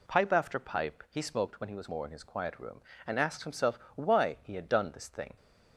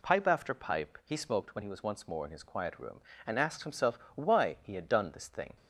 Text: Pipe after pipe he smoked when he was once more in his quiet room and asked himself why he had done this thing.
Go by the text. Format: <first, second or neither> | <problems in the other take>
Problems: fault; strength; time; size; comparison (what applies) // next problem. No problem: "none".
second | skips "once"; at 1.8 s // pauses between "himself" and "why"; slight; at 3.7 s; 0.18 s long; slight in the second